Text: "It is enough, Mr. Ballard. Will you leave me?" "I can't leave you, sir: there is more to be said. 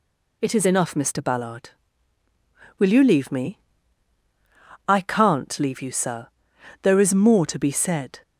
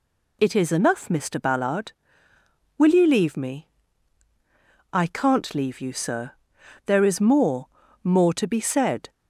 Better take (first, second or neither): first